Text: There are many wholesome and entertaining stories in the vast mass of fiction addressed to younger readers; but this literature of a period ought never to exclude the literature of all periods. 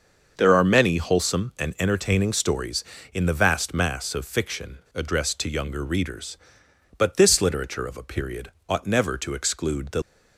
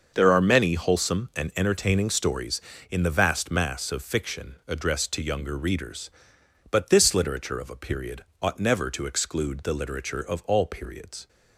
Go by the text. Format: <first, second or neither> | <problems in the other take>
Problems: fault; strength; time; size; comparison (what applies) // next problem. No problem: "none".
second | starts louder than the rest; until 1.3 s; 6 dB; also in the second // pauses between "fiction" and "addressed"; slight; at 4.7 s; 0.16 s long // pauses between "period" and "ought"; slight; at 8.4 s; 0.16 s long; slight in the second // stops before "literature of all periods"; at 10.0 s